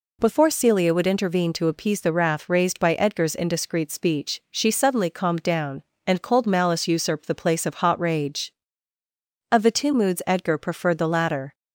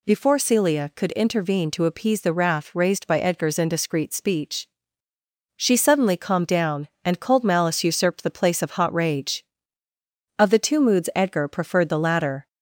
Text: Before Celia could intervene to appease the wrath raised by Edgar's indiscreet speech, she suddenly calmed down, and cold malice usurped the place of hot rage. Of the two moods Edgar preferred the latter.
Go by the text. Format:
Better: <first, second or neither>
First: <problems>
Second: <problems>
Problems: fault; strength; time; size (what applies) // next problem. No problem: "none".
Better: second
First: says "would" for "could"; at 0.9 s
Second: none